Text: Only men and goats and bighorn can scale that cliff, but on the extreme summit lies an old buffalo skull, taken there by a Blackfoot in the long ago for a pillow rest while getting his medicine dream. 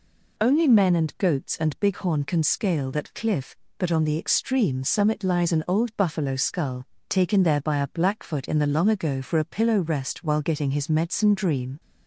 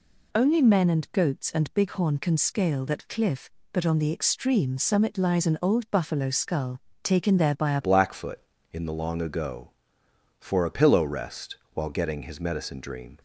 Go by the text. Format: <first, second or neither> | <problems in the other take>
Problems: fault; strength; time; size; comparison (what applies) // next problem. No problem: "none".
first | changes voice at "Blackfoot"; from 7.8 s on; 5.3 s long // pauses between "rest" and "while"; slight; at 11.5 s; 0.18 s long